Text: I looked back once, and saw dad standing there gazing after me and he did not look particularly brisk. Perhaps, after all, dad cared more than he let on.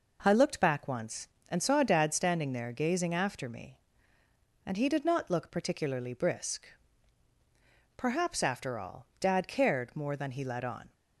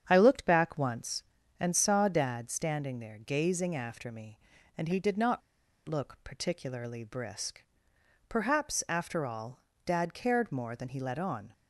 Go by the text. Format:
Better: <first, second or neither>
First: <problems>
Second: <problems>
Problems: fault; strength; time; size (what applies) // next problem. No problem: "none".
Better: first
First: none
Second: starts louder than the rest; strong; until 1.0 s; 8 dB // pauses between "not" and "look"; at 5.4 s; 0.45 s long